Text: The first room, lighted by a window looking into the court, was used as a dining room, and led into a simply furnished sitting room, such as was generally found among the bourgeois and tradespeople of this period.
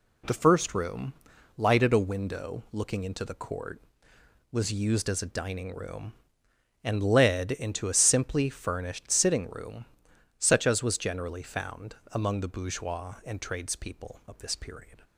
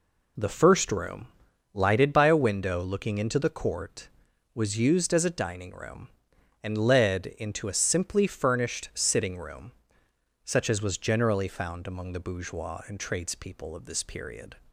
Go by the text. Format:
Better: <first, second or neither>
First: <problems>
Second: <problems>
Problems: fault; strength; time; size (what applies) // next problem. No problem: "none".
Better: second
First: skips "by"; at 1.9 s // pauses between "found" and "among"; slight; at 11.9 s; 0.16 s long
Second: none